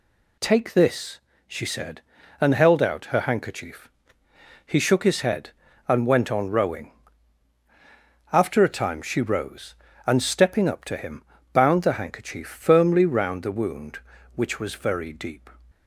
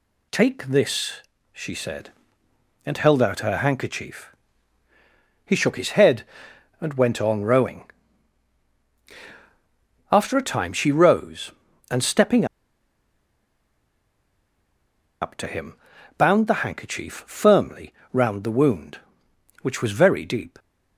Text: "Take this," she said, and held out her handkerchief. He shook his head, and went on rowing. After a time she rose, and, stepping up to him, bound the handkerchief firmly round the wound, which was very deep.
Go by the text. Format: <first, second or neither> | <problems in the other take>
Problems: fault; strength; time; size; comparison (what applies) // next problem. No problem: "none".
first | pauses between "stepping" and "up"; strong; at 12.4 s; 2.7 s long // pauses between "firmly" and "round"; slight; at 17.9 s; 0.20 s long